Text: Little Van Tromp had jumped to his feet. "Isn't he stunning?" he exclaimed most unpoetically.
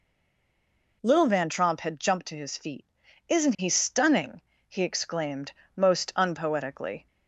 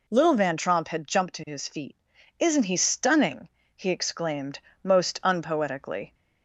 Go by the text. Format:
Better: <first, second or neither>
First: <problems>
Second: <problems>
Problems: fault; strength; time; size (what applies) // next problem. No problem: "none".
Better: second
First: stays silent before the first word; until 1.0 s; 1.0 s long // pauses between "exclaimed" and "most"; slight; at 5.5 s; 0.24 s long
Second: pauses between "exclaimed" and "most"; slight; at 4.5 s; 0.24 s long